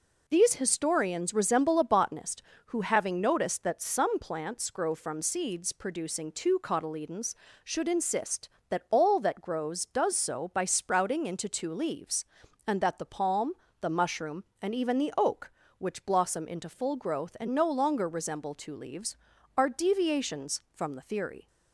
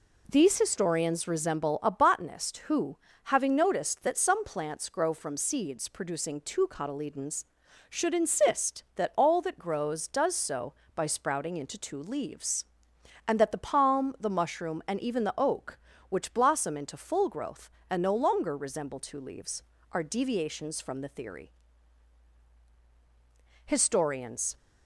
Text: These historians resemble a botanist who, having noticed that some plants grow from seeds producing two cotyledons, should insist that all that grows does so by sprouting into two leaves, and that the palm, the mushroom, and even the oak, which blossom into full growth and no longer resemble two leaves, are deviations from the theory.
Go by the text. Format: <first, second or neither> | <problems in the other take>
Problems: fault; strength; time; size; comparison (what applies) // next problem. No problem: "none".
first | goes on to say "Historians"; noticeable; from 23.6 s on; 0.92 s long